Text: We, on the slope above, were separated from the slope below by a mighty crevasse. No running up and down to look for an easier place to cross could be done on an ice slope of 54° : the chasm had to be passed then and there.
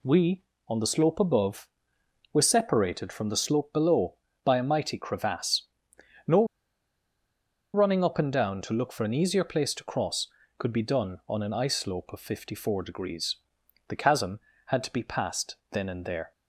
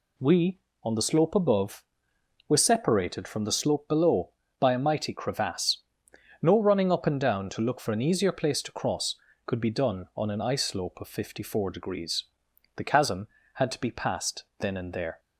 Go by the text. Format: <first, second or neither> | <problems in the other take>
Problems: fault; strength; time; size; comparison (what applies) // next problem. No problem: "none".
second | pauses between "No" and "running"; strong; at 6.4 s; 1.2 s long // pauses between "passed" and "then"; slight; at 15.5 s; 0.16 s long; slight in the second